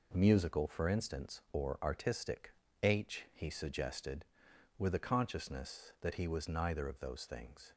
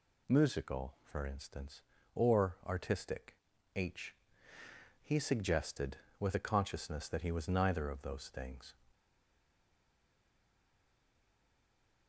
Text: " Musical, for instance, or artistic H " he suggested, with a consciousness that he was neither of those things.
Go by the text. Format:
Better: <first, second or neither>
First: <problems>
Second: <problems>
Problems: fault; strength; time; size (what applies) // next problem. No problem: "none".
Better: first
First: pauses between "artistic" and "H"; slight; at 2.5 s; 0.31 s long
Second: pauses between "artistic" and "H"; at 3.3 s; 0.40 s long // stays silent after the last word; strong; from 8.9 s on; 3.1 s long